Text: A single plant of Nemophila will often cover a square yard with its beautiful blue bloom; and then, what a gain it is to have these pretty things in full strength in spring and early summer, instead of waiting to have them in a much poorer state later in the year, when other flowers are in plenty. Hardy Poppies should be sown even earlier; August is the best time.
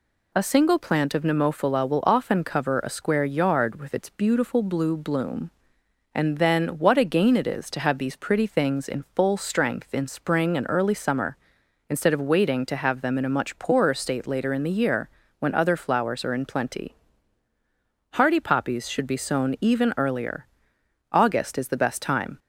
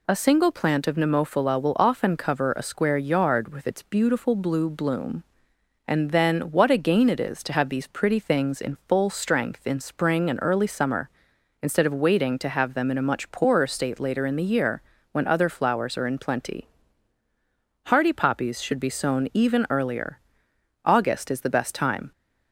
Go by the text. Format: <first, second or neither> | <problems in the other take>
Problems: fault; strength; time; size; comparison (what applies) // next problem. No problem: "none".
neither | none